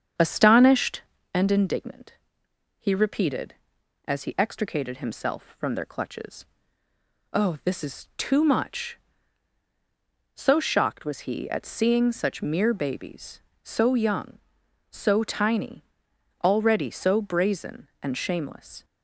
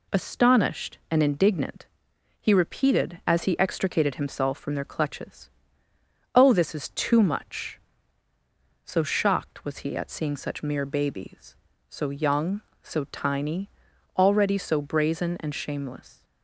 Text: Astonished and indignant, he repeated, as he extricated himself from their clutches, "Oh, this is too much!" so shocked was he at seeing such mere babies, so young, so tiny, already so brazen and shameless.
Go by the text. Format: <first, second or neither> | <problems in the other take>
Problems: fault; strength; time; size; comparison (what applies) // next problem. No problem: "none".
second | starts louder than the rest; strong; until 1.2 s; 7.5 dB